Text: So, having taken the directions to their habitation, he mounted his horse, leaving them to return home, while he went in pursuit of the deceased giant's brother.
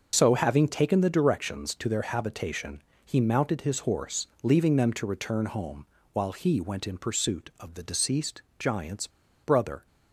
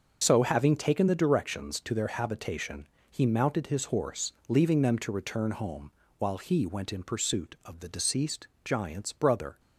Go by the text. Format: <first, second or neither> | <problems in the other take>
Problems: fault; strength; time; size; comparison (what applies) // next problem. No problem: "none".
second | starts louder than the rest; until 1.2 s; 6.5 dB; also in the second // pauses between "deceased" and "giant's"; slight; at 8.4 s; 0.16 s long; slight in the second // pauses between "giant's" and "brother"; slight; at 9.0 s; 0.34 s long